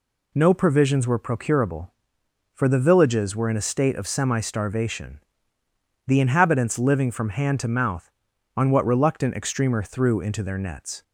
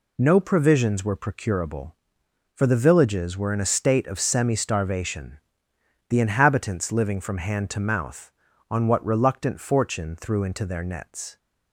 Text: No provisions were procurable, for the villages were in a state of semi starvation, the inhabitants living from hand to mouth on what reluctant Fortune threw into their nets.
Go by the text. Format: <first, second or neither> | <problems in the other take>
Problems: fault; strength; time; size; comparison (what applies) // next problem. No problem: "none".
second | says "Extremer" for "Fortune"; at 9.3 s